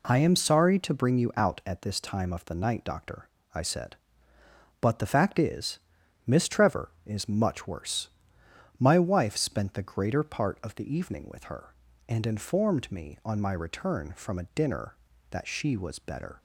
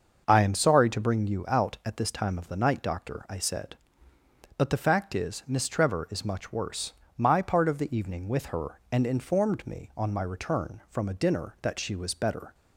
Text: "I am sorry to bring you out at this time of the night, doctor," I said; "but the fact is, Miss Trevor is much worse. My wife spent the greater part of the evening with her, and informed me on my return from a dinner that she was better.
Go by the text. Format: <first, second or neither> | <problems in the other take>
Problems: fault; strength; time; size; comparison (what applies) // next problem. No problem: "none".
first | starts louder than the rest; until 1.2 s; 6 dB // skips "wife spent the greater"; at 7.4 s